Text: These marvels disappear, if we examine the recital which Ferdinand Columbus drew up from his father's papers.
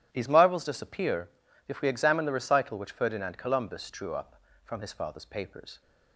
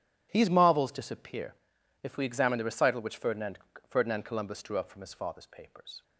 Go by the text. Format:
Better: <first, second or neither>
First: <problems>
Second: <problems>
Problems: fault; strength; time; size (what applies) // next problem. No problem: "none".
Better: first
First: none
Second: says "Ferdinand" twice; at 3.8 s